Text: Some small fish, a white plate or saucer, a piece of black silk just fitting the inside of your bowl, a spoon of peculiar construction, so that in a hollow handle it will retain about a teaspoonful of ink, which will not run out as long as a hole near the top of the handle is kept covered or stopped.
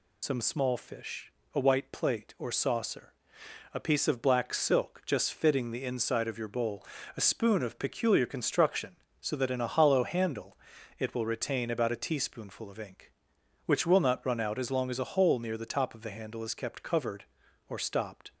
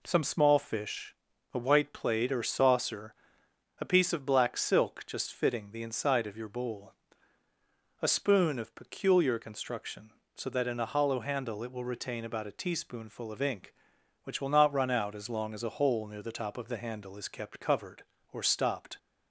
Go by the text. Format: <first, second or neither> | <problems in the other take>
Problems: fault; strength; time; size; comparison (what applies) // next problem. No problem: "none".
second | loses the start of "Some"; at 0.2 s; 75 ms // pauses between "handle" and "it"; at 10.5 s; 0.44 s long